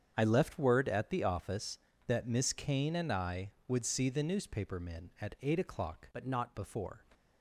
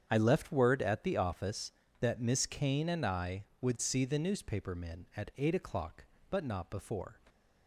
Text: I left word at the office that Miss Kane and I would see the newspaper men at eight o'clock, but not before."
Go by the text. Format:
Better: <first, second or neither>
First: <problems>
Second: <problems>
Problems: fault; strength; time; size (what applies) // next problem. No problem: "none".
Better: second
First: starts louder than the rest; strong; until 1.1 s; 7.5 dB // changes voice from "but" to "not"; from 6.1 to 6.5 s; 0.4 s long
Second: starts louder than the rest; strong; until 1.1 s; 8 dB